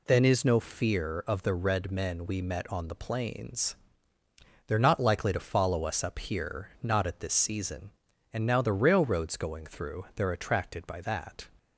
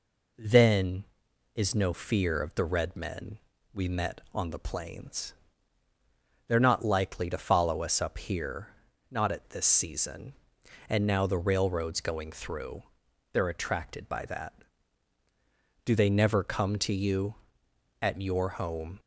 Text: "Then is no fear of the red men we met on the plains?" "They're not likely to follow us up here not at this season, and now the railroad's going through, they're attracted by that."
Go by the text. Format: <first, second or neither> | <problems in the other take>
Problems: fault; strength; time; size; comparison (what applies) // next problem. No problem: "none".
first | pauses between "men" and "we"; slight; at 3.3 s; 0.34 s long // pauses between "here" and "not"; at 8.6 s; 0.42 s long // goes on to say "Do they never come to you at your home"; strong; from 15.8 s on; 3.1 s long